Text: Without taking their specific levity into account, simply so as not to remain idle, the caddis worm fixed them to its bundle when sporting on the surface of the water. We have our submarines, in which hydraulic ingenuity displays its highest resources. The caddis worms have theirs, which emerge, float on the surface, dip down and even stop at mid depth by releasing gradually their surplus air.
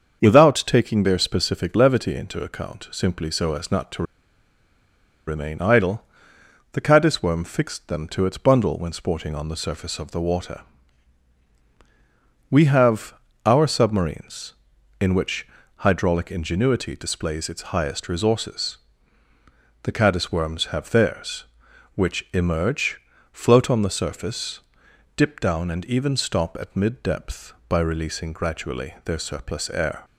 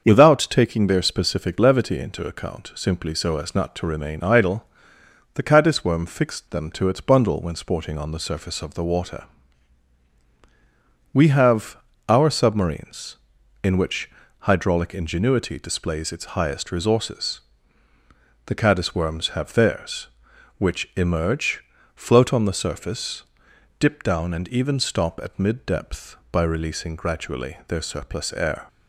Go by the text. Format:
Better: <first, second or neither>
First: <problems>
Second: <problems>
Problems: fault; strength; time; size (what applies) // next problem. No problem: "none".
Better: second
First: starts louder than the rest; until 1.2 s; 7 dB // pauses between "to" and "remain"; strong; at 4.0 s; 1.2 s long // pauses between "have" and "our"; slight; at 13.1 s; 0.32 s long // pauses between "which" and "hydraulic"; slight; at 15.4 s; 0.28 s long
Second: starts louder than the rest; until 1.0 s; 7 dB // pauses between "have" and "our"; slight; at 11.7 s; 0.32 s long // pauses between "which" and "hydraulic"; slight; at 14.1 s; 0.28 s long